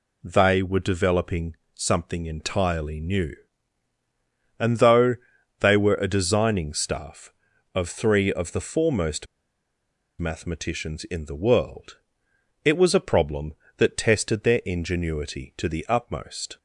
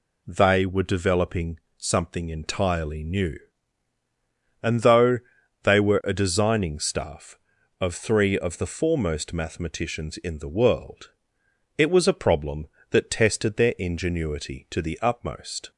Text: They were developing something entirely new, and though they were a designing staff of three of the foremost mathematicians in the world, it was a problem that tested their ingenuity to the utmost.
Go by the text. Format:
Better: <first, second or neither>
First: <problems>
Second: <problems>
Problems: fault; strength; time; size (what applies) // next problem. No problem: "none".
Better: second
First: pauses between "developing" and "something"; slight; at 1.5 s; 0.20 s long // pauses between "though" and "they"; noticeable; at 5.1 s; 0.46 s long // pauses between "foremost" and "mathematicians"; noticeable; at 9.2 s; 0.95 s long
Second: pauses between "developing" and "something"; slight; at 1.5 s; 0.20 s long // pauses between "though" and "they"; noticeable; at 5.1 s; 0.46 s long